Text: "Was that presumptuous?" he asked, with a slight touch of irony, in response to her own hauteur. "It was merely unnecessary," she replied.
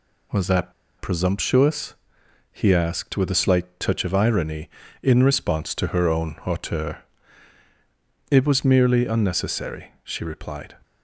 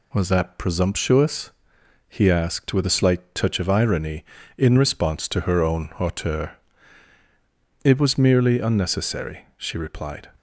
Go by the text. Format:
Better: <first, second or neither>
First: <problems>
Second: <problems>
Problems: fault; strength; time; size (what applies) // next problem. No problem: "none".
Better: second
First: pauses between "that" and "presumptuous"; slight; at 0.7 s; 0.26 s long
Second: none